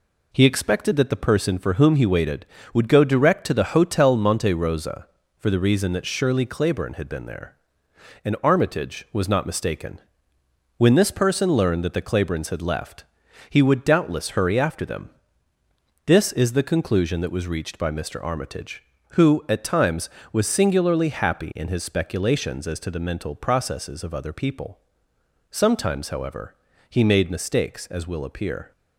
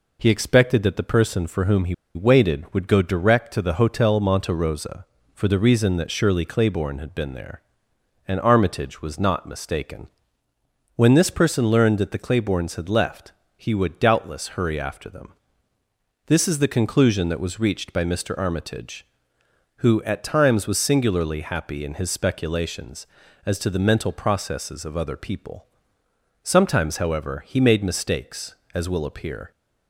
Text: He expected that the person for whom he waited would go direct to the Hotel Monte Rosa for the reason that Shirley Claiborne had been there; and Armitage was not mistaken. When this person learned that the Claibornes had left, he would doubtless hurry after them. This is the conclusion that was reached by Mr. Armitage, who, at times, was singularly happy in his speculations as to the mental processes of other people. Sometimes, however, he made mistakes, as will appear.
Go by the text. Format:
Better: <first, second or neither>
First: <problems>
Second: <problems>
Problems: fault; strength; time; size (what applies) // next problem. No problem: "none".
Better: first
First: none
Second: pauses between "he" and "waited"; slight; at 1.9 s; 0.20 s long